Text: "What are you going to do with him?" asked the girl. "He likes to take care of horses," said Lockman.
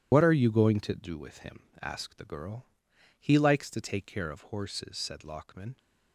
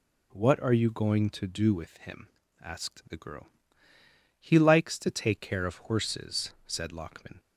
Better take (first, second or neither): second